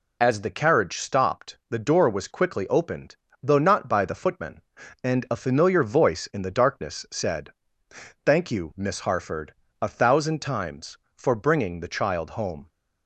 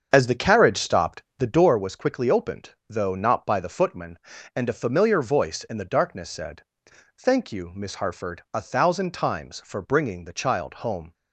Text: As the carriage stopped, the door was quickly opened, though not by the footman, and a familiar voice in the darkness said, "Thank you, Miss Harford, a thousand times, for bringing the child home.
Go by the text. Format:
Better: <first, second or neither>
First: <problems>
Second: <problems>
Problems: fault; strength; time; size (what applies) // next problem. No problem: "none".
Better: first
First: none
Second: starts louder than the rest; until 1.7 s; 7 dB